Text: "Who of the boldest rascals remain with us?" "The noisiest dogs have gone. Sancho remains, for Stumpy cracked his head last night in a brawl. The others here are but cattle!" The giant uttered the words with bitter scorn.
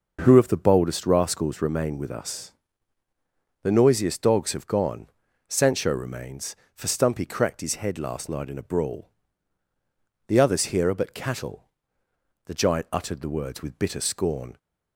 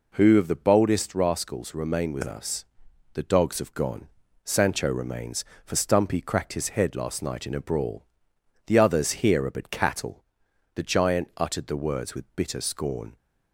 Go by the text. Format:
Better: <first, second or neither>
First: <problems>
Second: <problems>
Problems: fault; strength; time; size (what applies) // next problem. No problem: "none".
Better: first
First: none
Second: skips "noisiest"; at 3.2 s